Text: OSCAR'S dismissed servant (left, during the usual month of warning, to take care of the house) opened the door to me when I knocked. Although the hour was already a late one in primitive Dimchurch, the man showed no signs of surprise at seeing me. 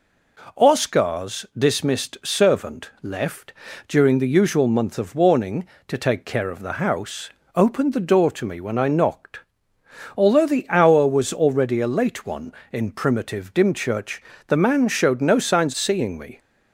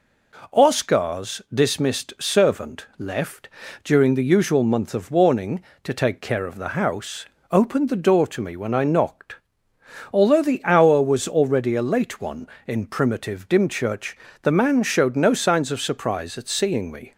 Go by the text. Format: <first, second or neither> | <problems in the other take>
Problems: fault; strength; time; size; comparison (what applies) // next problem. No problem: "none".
second | skips "of surprise at"; at 15.7 s